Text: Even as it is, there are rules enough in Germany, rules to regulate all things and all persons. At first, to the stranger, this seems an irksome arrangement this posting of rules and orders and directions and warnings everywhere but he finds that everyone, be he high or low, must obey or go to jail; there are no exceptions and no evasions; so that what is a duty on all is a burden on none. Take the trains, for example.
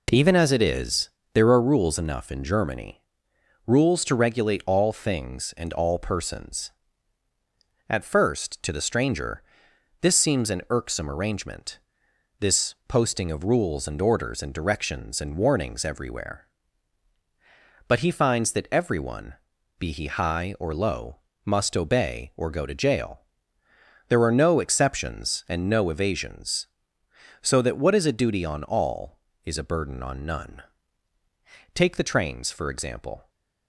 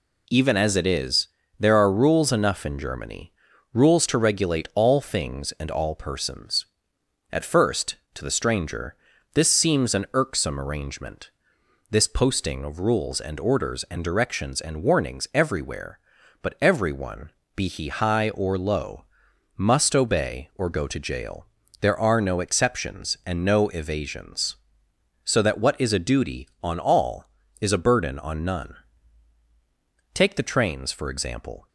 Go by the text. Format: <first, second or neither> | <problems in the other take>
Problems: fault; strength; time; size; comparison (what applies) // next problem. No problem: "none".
first | pauses between "arrangement" and "this"; noticeable; at 11.2 s; 0.60 s long; noticeable in the first // skips "he finds that"; at 16.5 s